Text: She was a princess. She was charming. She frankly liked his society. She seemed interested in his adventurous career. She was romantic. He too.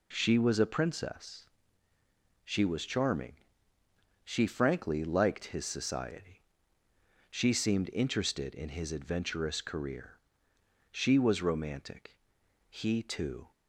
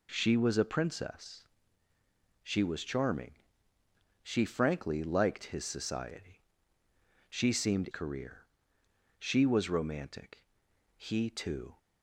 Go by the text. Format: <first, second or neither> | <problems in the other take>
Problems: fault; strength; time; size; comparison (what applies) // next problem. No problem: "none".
first | skips "interested in his adventurous"; at 7.8 s